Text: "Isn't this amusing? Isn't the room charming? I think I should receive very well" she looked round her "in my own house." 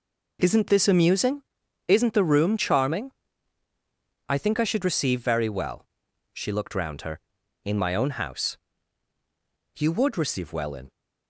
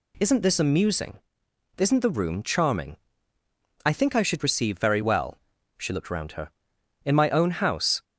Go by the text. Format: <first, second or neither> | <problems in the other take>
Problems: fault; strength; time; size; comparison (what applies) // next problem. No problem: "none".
second | pauses between "well" and "she"; noticeable; at 5.8 s; 0.48 s long; slight in the second // goes on to say "You would receive well in"; noticeable; from 9.7 s on; 1.1 s long